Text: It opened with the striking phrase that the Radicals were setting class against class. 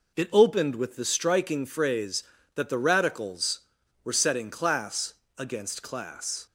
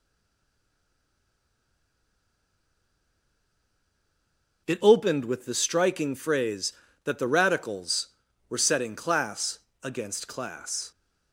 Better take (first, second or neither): first